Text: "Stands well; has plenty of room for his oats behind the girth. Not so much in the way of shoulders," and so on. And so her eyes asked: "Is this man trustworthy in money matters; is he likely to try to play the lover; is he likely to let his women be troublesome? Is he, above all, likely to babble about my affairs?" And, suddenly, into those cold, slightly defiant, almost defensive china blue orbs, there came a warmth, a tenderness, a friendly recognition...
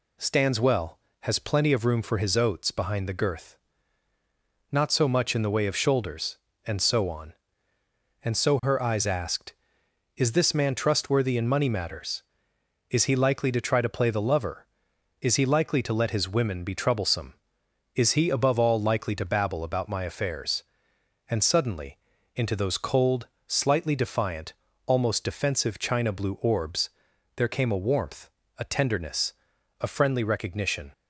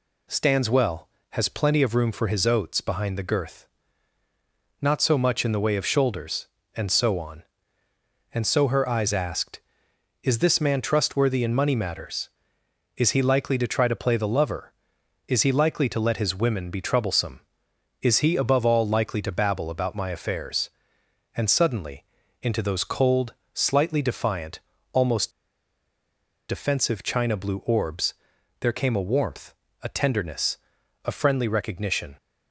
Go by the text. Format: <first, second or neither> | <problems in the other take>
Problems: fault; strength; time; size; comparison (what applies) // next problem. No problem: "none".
first | pauses between "almost" and "defensive"; at 25.2 s; 1.1 s long